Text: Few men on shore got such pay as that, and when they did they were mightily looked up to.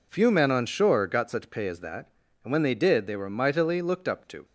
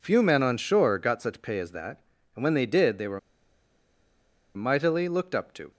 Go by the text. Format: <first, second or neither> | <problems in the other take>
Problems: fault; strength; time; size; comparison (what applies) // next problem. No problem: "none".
first | pauses between "were" and "mightily"; strong; at 3.1 s; 1.3 s long